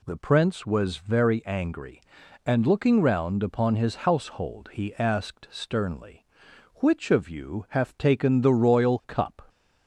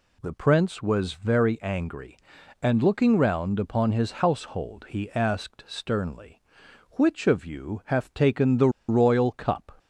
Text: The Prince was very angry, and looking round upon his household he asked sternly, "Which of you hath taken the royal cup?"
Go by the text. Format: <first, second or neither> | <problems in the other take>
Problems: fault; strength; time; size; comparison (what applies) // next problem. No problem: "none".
first | pauses between "the" and "royal"; slight; at 8.6 s; 0.19 s long